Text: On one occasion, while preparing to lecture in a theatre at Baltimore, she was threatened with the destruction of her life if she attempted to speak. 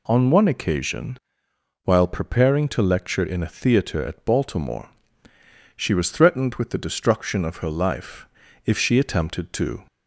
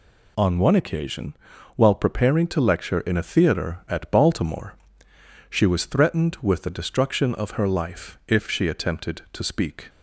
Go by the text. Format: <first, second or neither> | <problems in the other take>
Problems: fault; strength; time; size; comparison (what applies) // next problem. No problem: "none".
second | pauses between "life" and "if"; at 8.2 s; 0.38 s long // stops before "speak"; at 9.8 s